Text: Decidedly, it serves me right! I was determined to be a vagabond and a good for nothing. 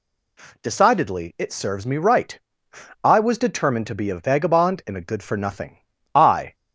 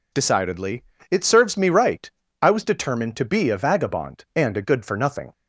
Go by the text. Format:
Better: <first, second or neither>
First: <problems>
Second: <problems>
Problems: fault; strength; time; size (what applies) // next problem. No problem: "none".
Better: second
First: goes on to say "I"; slight; from 6.1 s on; 0.42 s long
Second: none